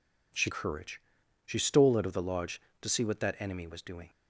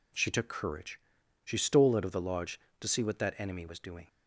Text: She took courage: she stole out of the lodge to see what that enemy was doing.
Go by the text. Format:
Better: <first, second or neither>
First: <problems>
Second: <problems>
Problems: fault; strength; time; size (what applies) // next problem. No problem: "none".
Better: second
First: skips "took"; at 0.4 s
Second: none